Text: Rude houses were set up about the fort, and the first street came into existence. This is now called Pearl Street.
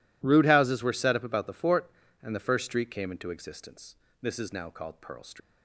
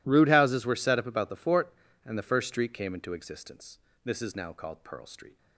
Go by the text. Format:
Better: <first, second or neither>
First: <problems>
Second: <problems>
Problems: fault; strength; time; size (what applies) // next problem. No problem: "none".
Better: second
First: leaves "Street" unfinished; at 5.4 s; 140 ms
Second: none